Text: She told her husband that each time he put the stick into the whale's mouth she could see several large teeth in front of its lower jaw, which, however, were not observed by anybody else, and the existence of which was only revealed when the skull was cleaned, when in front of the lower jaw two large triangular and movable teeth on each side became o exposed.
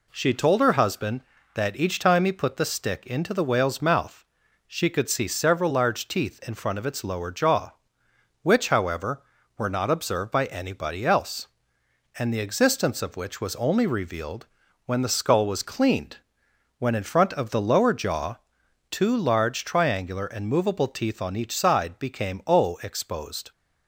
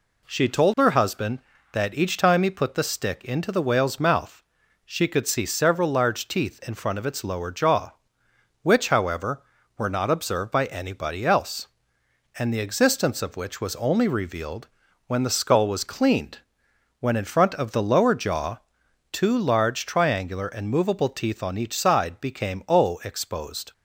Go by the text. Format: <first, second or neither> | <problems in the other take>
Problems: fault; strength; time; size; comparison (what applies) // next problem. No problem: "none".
neither | pauses between "mouth" and "she"; noticeable; the same in both // pauses between "revealed" and "when"; the same in both // pauses between "jaw" and "two"; noticeable; the same in both